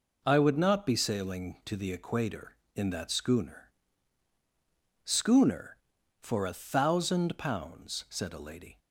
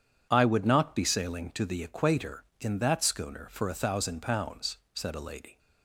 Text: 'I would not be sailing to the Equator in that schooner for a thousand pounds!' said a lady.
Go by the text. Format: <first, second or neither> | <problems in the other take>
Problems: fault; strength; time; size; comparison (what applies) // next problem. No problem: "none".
second | says "schooner" twice; at 5.0 s